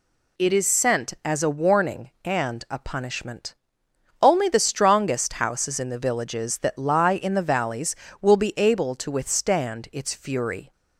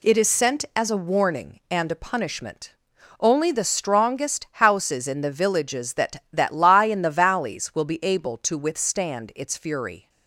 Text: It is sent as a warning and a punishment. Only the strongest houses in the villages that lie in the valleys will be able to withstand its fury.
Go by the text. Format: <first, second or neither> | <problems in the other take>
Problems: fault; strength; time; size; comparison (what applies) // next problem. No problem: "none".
first | says "that" twice; at 6.3 s